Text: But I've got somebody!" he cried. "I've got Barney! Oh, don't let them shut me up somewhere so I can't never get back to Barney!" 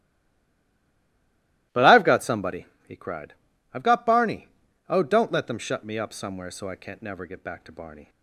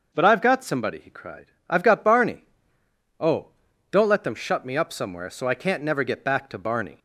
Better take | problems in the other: second | stays silent before the first word; noticeable; until 1.7 s; 1.7 s long // starts louder than the rest; strong; until 2.9 s; 18 dB

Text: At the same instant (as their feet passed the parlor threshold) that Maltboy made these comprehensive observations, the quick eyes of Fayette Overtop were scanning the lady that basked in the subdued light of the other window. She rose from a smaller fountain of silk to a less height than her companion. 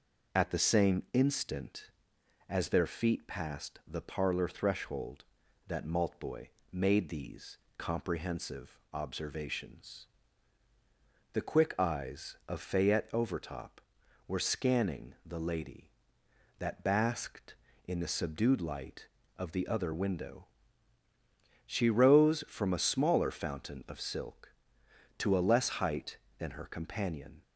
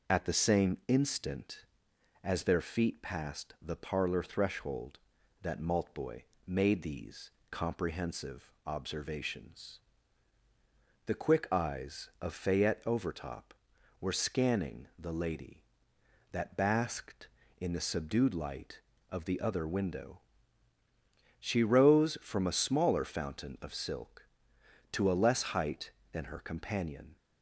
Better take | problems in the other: neither | pauses between "Maltboy" and "made"; slight; the same in both // pauses between "these" and "comprehensive"; slight; the same in both

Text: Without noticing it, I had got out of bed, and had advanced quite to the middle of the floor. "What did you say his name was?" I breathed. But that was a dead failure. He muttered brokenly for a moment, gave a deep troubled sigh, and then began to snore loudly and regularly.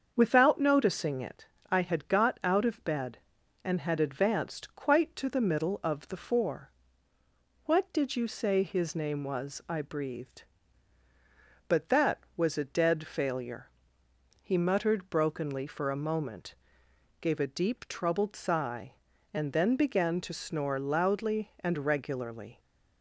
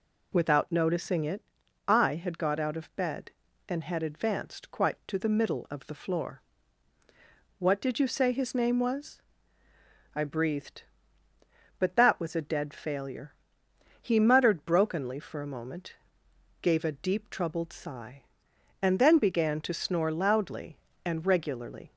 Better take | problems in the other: second | starts louder than the rest; until 1.1 s; 7 dB // says "four" for "floor"; at 6.1 s

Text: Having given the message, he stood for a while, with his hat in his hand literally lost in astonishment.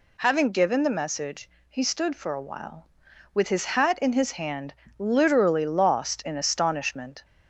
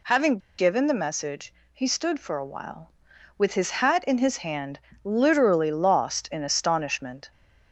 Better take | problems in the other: first | pauses between "Having" and "given"; slight; at 0.3 s; 0.19 s long // pauses between "hand" and "literally"; slight; at 4.8 s; 0.24 s long; slight in the first

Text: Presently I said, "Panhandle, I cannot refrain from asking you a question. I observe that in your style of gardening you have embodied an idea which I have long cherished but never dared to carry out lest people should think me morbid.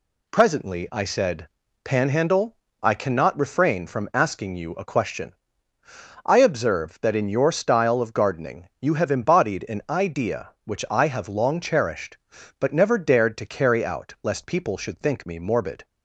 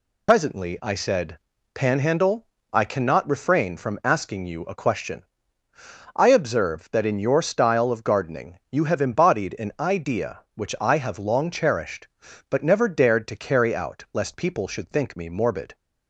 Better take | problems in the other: first | loses the start of "Presently"; at 0.2 s; 90 ms

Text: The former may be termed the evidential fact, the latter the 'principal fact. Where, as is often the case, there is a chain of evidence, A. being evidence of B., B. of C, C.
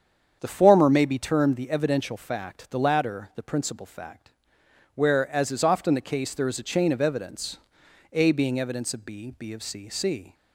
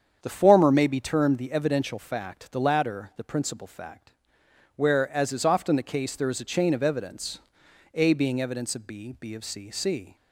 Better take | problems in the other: neither | starts louder than the rest; strong; the same in both

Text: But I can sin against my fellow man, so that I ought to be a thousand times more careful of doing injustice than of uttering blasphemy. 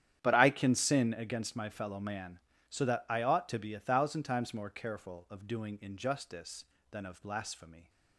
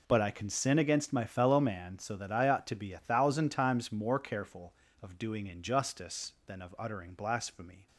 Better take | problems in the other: second | starts louder than the rest; strong; until 1.2 s; 10 dB // skips "uttering"; at 7.2 s

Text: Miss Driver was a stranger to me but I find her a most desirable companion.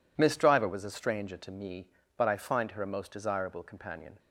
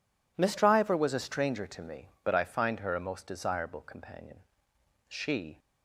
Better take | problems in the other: first | goes on to say "She"; from 5.0 s on; 0.52 s long

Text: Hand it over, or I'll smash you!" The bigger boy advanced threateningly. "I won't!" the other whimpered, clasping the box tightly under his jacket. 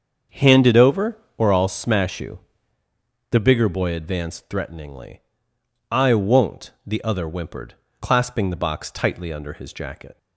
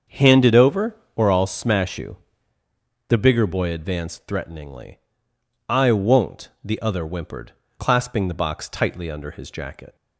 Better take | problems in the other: neither | starts louder than the rest; the same in both

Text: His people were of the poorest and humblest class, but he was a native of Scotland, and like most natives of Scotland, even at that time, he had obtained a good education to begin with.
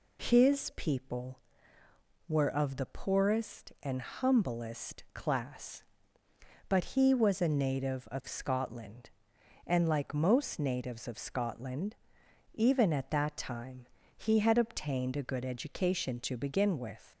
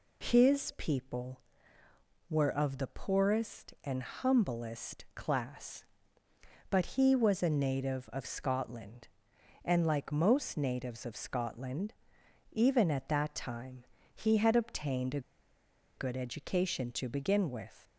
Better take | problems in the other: first | pauses between "a" and "good"; noticeable; at 15.1 s; 0.76 s long

